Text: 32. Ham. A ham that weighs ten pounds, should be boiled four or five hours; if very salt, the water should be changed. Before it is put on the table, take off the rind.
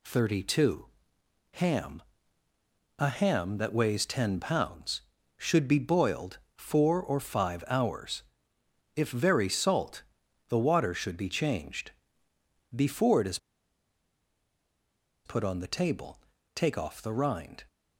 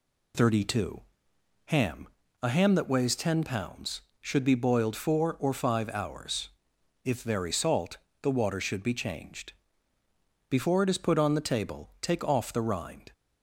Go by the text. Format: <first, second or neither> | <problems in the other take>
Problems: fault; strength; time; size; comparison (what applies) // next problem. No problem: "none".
second | pauses between "boiled" and "four"; slight; at 6.3 s; 0.18 s long // pauses between "is" and "put"; strong; at 13.3 s; 1.8 s long